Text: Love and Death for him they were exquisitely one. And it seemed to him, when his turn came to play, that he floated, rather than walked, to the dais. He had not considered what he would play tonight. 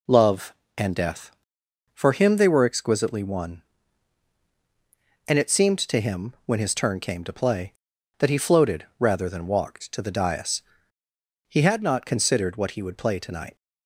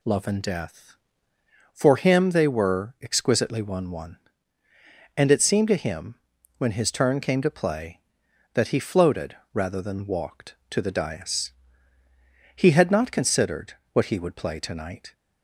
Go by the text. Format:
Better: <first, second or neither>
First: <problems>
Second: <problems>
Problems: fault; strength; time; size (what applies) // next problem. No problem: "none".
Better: first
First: none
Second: says "one" twice; at 3.8 s // pauses between "considered" and "what"; slight; at 13.7 s; 0.20 s long